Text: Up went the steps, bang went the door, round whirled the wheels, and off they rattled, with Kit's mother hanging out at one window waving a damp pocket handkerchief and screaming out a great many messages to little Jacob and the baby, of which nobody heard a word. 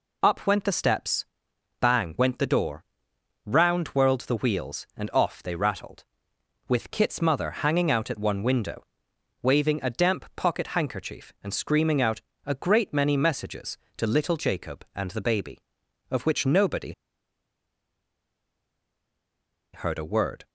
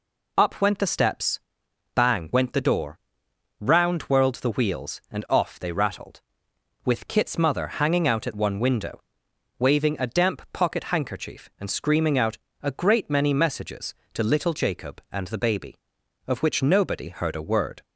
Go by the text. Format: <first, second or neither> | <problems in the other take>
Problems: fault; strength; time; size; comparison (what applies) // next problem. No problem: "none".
second | pauses between "window" and "waving"; noticeable; at 8.8 s; 0.60 s long; noticeable in the second // pauses between "out" and "a"; slight; at 12.1 s; 0.24 s long; slight in the second // pauses between "nobody" and "heard"; strong; at 16.9 s; 2.8 s long